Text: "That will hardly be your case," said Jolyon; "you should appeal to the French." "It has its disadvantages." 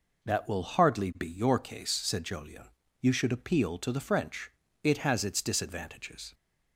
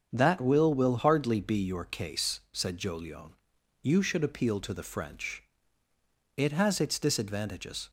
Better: first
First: none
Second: starts louder than the rest; strong; until 1.1 s; 7 dB // says "will" twice; at 0.7 s

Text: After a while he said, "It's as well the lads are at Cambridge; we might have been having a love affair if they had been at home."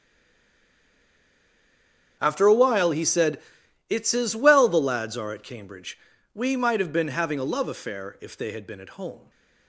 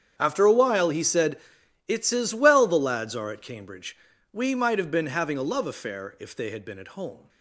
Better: second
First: stays silent before the first word; until 2.1 s; 2.1 s long // starts louder than the rest; strong; until 3.2 s; 8 dB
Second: starts louder than the rest; strong; until 1.1 s; 8 dB

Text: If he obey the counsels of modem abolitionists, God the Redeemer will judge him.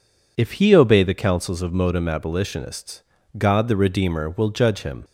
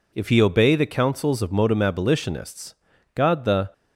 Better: first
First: none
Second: stops before "Redeemer will judge him"; at 3.7 s

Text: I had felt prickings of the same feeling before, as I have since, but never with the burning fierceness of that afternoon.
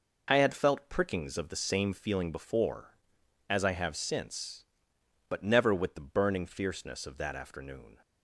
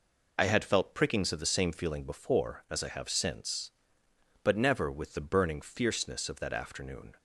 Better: first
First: none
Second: loses the start of "I"; at 0.3 s; 20 ms

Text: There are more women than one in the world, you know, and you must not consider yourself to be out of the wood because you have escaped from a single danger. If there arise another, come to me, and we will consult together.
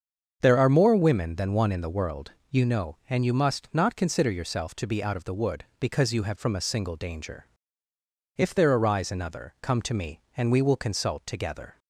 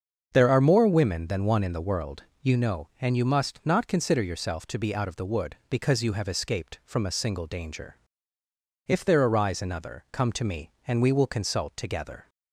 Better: second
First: starts louder than the rest; until 1.4 s; 6.5 dB // skips "escaped"; at 6.3 s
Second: starts louder than the rest; until 1.3 s; 7 dB

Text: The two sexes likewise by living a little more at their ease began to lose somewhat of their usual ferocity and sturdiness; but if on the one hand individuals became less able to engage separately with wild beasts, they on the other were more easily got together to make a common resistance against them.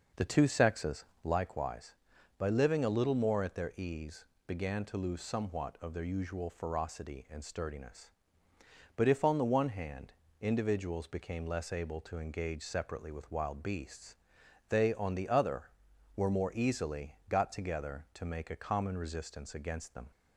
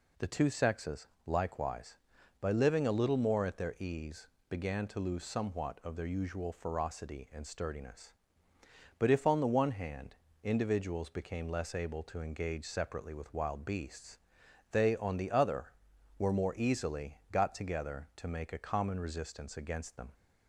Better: second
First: starts louder than the rest; noticeable; until 1.3 s; 5.5 dB // pauses between "sexes" and "likewise"; slight; at 1.0 s; 0.18 s long // pauses between "ease" and "began"; slight; at 4.2 s; 0.20 s long // pauses between "hand" and "individuals"; slight; at 10.1 s; 0.26 s long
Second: pauses between "sexes" and "likewise"; slight; at 1.0 s; 0.18 s long // pauses between "ease" and "began"; slight; at 4.2 s; 0.20 s long // pauses between "hand" and "individuals"; slight; at 10.1 s; 0.26 s long

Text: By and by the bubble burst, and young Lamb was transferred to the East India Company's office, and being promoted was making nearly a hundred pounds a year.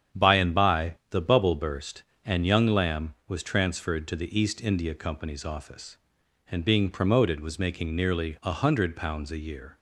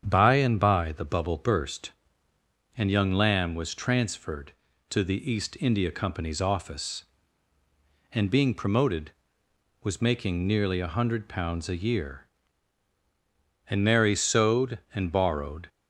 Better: first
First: starts louder than the rest; strong; until 1.2 s; 8 dB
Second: starts louder than the rest; strong; until 1.0 s; 8 dB // goes on to say "And Mary sewed and borrowed"; strong; from 13.6 s on; 2.0 s long

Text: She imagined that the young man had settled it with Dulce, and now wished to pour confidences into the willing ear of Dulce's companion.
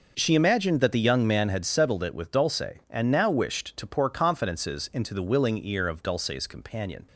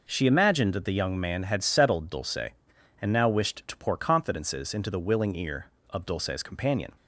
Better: first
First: none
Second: skips "it with"; at 2.0 s

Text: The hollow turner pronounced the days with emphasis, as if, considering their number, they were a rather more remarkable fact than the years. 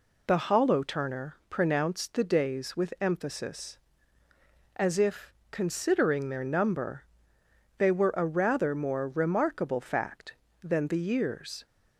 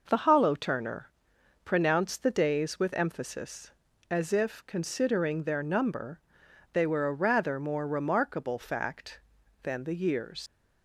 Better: first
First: pauses between "turner" and "pronounced"; slight; at 1.3 s; 0.16 s long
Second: pauses between "turner" and "pronounced"; noticeable; at 1.1 s; 0.54 s long // leaves "years" unfinished; at 10.4 s; 120 ms

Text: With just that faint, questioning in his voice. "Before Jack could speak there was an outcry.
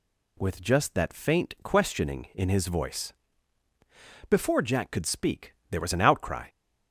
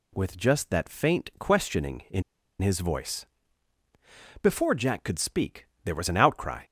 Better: first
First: pauses between "speak" and "there"; slight; at 5.5 s; 0.18 s long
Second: pauses between "in" and "his"; at 2.2 s; 0.38 s long // pauses between "speak" and "there"; slight; at 5.6 s; 0.20 s long

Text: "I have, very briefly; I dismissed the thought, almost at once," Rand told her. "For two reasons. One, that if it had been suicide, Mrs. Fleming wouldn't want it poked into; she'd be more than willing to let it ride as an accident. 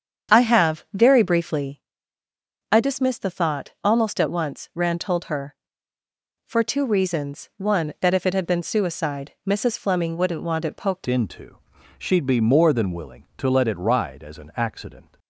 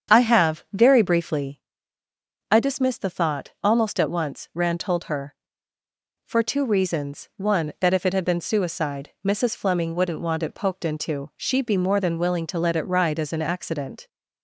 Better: second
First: starts louder than the rest; strong; until 1.4 s; 7.5 dB // changes voice at "into"; from 11.0 s on; 4.1 s long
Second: starts louder than the rest; strong; until 1.2 s; 7.5 dB

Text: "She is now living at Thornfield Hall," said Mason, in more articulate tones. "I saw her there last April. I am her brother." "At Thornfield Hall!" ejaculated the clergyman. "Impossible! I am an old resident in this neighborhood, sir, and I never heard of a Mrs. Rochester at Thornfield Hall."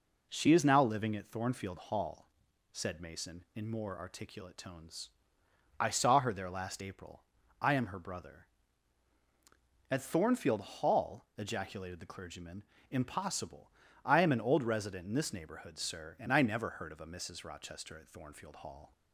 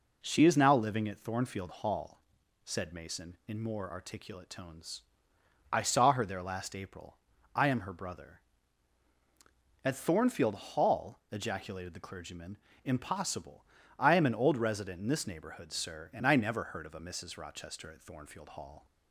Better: neither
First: none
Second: none

